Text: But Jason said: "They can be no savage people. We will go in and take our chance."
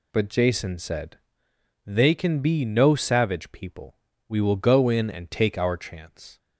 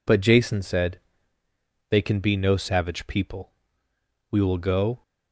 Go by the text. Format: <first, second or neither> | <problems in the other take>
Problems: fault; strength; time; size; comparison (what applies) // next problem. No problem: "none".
first | stops before "in and take our chance"; at 5.0 s